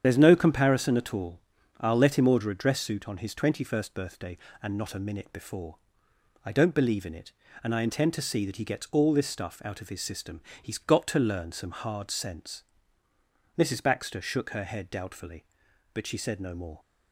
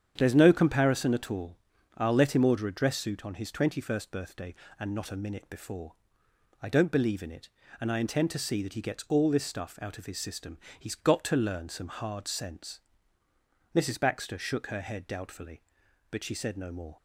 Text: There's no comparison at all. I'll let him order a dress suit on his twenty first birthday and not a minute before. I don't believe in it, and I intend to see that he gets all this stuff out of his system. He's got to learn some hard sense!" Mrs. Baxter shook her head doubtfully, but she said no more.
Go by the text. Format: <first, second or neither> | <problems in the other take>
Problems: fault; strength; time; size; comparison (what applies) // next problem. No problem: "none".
second | loses the start of "There's"; at 0.0 s; 65 ms // starts louder than the rest; strong; until 1.0 s; 8.5 dB; strong in the second